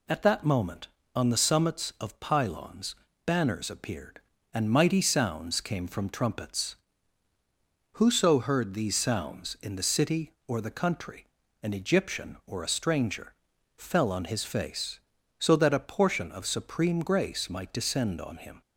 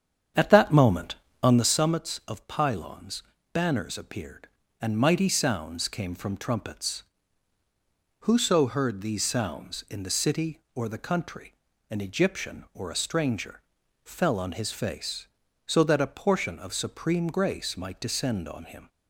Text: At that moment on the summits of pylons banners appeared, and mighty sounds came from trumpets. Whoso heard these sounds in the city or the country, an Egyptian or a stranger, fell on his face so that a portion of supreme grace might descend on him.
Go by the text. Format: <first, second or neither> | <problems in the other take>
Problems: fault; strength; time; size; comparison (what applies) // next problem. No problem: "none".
first | starts louder than the rest; strong; until 1.7 s; 8 dB // pauses between "pylons" and "banners"; slight; at 3.2 s; 0.30 s long; slight in the first